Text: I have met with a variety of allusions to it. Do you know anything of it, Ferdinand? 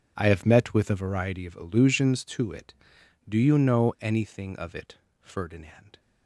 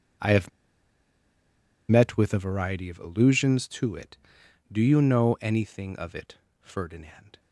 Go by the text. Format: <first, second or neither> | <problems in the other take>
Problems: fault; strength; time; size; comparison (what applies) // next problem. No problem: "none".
first | pauses between "have" and "met"; strong; at 0.4 s; 1.3 s long